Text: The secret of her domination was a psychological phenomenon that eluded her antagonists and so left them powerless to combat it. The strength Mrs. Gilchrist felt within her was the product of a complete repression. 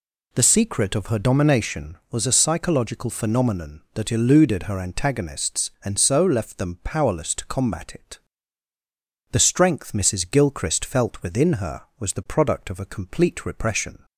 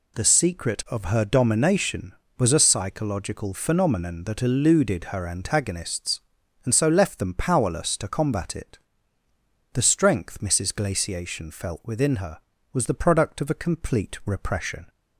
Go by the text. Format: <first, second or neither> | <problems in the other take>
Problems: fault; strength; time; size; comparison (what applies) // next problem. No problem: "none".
first | says "Glaciation" for "Gilchrist"; at 10.7 s